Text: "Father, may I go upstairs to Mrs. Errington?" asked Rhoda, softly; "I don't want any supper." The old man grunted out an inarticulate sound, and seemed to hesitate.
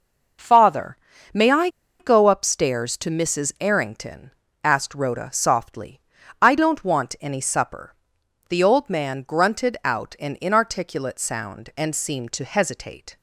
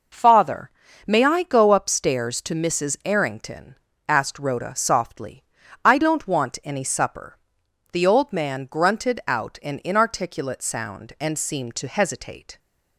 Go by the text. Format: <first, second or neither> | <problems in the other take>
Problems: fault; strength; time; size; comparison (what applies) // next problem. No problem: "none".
second | pauses between "I" and "go"; slight; at 1.6 s; 0.31 s long